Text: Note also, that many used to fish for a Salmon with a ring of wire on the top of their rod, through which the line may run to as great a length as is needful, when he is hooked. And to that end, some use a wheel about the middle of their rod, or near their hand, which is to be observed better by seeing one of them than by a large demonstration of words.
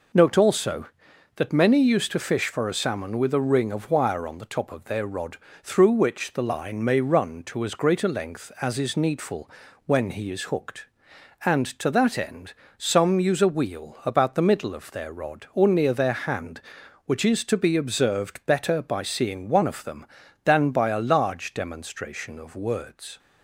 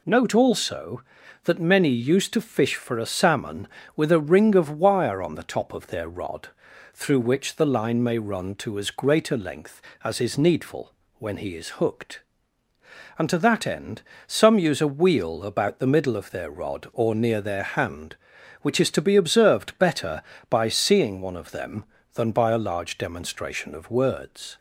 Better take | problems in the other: neither | none

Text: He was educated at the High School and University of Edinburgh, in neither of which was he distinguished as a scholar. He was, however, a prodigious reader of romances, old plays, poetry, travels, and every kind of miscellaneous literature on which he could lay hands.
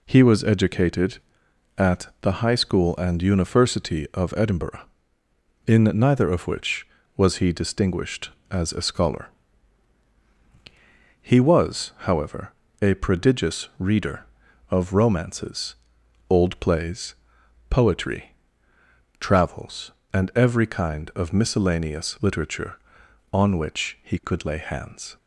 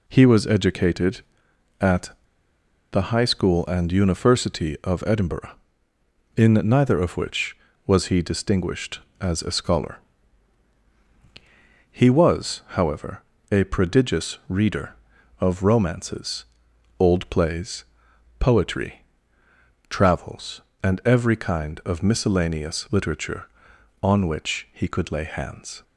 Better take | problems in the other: first | pauses between "at" and "the"; noticeable; at 2.1 s; 0.82 s long

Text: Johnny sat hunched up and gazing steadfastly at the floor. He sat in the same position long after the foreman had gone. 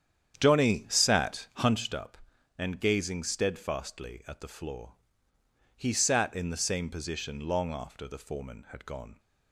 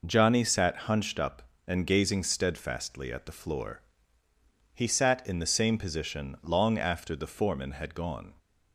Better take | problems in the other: second | starts louder than the rest; strong; until 1.9 s; 9 dB

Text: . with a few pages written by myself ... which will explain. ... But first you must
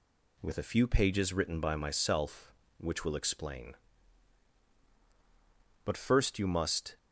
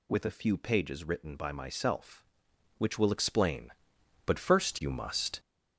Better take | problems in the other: first | gets louder; throughout; 7 dB

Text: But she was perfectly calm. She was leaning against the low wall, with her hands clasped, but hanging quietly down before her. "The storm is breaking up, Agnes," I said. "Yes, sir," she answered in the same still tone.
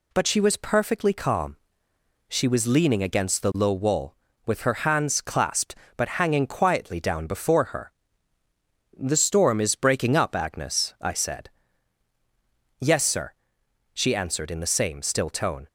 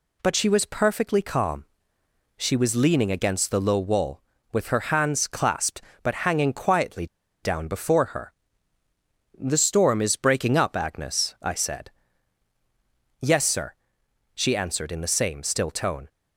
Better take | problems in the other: first | pauses between "quietly" and "down"; at 7.0 s; 0.37 s long

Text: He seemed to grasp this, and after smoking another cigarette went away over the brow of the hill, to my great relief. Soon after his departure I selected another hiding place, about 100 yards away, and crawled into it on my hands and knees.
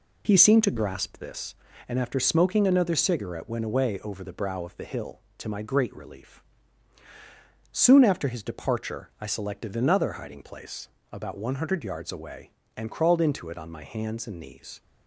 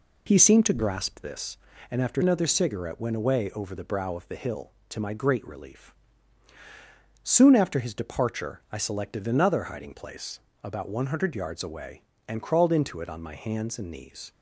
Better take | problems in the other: first | skips "smoking"; at 2.2 s

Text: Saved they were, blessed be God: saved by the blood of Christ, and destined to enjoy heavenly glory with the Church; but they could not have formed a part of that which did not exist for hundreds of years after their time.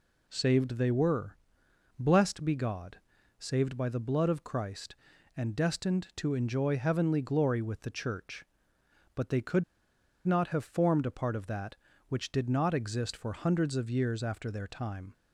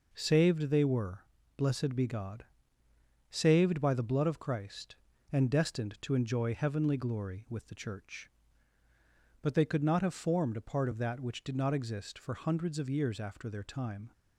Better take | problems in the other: second | pauses between "could" and "not"; noticeable; at 9.6 s; 0.62 s long

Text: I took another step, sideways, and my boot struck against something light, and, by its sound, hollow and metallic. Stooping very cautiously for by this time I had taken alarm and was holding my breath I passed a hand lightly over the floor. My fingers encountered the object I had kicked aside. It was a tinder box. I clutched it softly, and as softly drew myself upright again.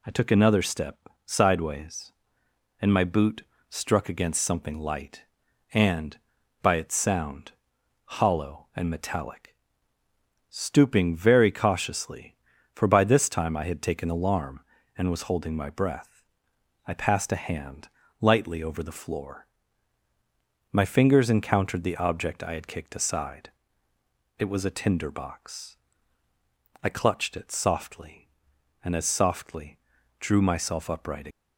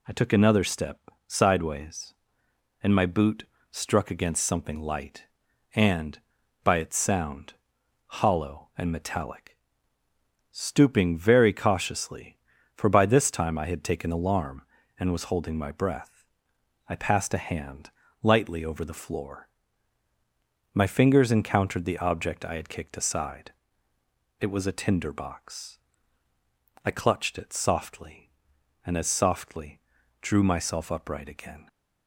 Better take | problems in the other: second | pauses between "boot" and "struck"; slight; at 3.4 s; 0.26 s long; slight in the second // pauses between "breath" and "I"; noticeable; at 16.2 s; 0.64 s long; noticeable in the second // pauses between "hand" and "lightly"; slight; at 17.8 s; 0.32 s long; slight in the second // pauses between "softly" and "drew"; at 29.7 s; 0.42 s long; also in the second // stops before "again"; at 31.2 s

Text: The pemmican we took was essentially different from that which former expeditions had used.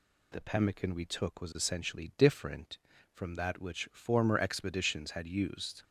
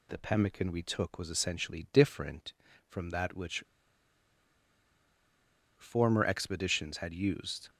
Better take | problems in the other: first | pauses between "which" and "former"; strong; at 3.6 s; 2.1 s long

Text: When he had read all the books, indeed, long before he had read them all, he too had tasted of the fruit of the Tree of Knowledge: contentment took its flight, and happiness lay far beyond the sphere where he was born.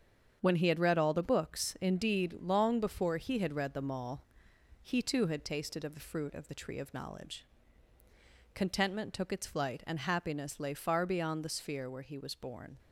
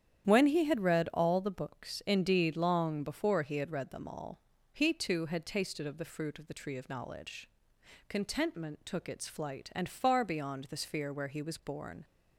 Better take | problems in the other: first | starts louder than the rest; strong; until 1.3 s; 9.5 dB; strong in the first // skips "happiness lay"; at 9.8 s

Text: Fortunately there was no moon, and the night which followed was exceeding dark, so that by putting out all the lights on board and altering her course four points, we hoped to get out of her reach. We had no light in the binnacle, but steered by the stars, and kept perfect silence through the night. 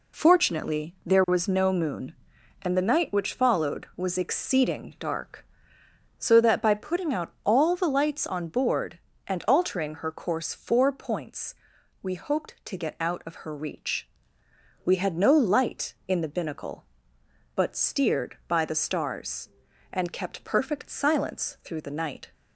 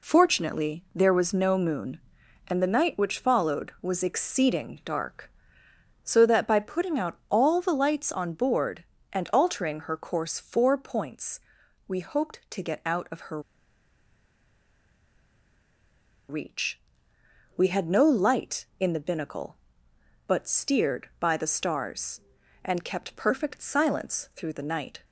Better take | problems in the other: first | pauses between "her" and "reach"; strong; at 13.3 s; 2.8 s long

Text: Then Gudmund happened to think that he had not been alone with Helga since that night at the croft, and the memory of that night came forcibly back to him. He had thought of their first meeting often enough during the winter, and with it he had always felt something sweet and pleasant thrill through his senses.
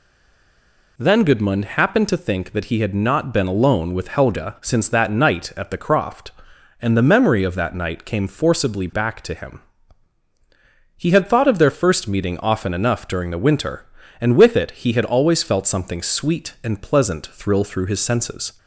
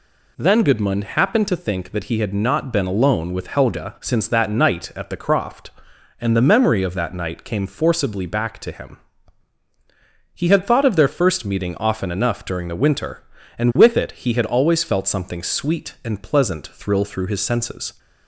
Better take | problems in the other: second | stays silent before the first word; until 0.9 s; 0.9 s long

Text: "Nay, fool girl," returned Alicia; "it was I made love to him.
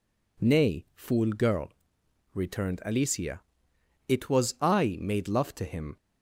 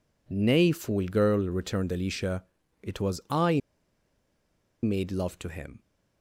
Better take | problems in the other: first | pauses between "I" and "made"; at 3.6 s; 1.2 s long

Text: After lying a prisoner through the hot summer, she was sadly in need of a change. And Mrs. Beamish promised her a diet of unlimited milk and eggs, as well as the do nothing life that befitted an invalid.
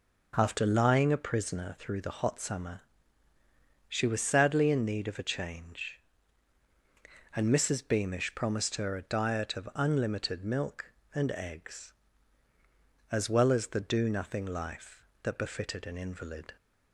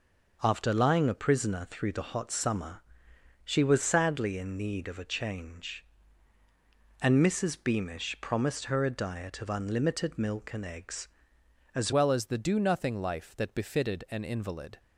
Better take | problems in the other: first | changes voice at "well"; from 11.9 s on; 2.8 s long

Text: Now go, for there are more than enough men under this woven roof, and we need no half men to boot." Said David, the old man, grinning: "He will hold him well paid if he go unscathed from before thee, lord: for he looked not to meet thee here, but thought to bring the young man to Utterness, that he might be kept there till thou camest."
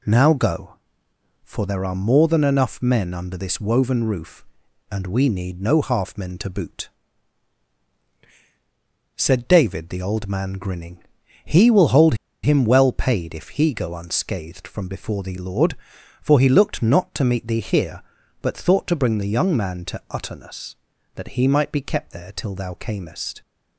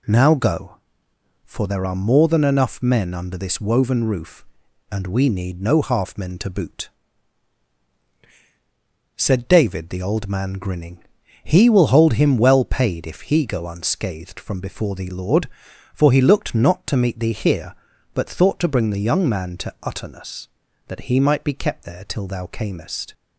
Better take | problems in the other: second | pauses between "hold" and "him"; slight; at 12.1 s; 0.29 s long

